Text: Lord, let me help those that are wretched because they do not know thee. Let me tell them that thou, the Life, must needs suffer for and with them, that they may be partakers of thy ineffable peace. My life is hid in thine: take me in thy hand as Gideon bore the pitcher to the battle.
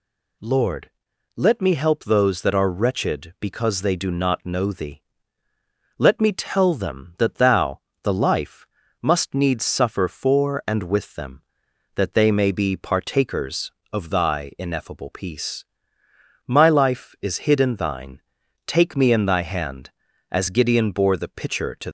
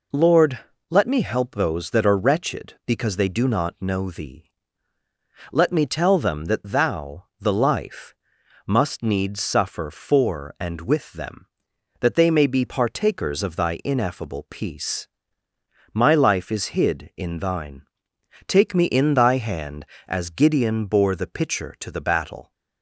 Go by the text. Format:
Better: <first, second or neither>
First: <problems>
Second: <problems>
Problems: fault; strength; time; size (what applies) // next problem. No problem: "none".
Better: second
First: stops before "the battle"; at 21.8 s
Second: none